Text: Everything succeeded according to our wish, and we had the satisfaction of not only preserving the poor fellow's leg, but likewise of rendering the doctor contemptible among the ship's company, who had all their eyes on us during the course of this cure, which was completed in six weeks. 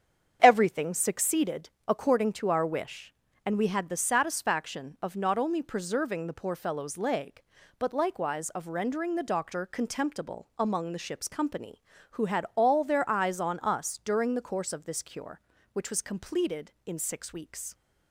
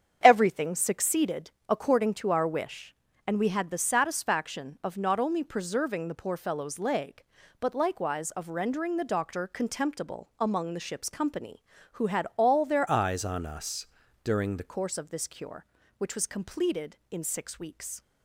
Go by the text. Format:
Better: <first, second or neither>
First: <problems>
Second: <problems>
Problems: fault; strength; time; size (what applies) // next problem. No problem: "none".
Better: first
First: starts louder than the rest; strong; until 1.4 s; 8 dB // pauses between "succeeded" and "according"; slight; at 1.6 s; 0.18 s long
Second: starts louder than the rest; strong; until 1.2 s; 8 dB // pauses between "succeeded" and "according"; slight; at 1.5 s; 0.18 s long // changes voice from "eyes" to "the"; from 12.8 to 14.7 s; 1.9 s long // pauses between "us" and "during"; at 13.8 s; 0.38 s long